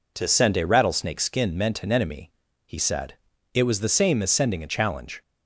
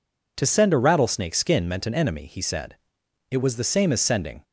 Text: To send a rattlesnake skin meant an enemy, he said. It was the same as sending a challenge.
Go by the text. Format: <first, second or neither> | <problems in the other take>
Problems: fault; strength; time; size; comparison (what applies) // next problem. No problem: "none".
first | stops before "a challenge"; at 4.4 s